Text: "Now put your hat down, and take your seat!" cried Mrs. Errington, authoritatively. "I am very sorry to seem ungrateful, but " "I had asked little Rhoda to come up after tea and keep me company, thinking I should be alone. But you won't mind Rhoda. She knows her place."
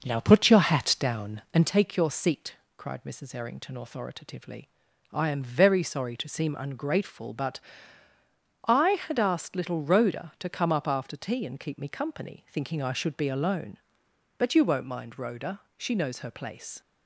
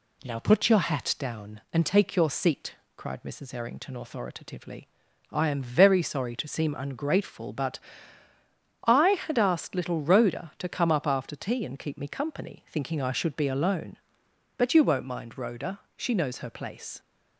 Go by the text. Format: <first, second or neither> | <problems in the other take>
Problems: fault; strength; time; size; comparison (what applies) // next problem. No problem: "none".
second | starts louder than the rest; noticeable; until 1.8 s; 6 dB